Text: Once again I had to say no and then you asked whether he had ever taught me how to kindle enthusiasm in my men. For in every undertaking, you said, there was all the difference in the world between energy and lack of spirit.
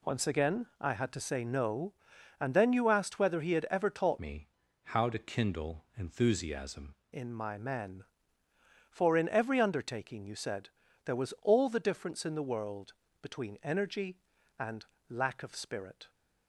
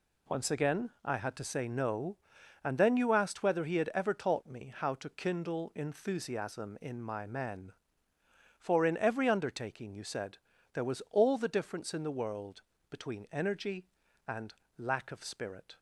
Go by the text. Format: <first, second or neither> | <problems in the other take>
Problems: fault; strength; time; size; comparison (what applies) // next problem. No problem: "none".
second | changes voice from "me" to "enthusiasm"; from 4.1 to 6.9 s; 2.8 s long // pauses between "me" and "how"; slight; at 4.4 s; 0.36 s long // pauses between "world" and "between"; slight; at 12.9 s; 0.30 s long; slight in the second // pauses between "and" and "lack"; slight; at 14.8 s; 0.24 s long; slight in the second